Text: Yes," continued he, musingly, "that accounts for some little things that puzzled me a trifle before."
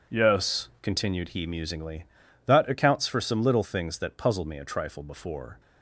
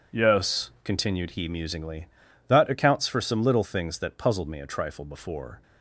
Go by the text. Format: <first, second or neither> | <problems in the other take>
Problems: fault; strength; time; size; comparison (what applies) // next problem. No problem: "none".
neither | none